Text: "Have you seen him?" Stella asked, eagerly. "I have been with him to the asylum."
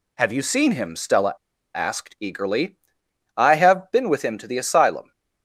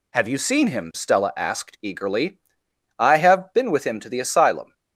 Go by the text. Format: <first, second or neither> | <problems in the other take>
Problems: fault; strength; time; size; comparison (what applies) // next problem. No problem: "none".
second | pauses between "Stella" and "asked"; at 1.3 s; 0.42 s long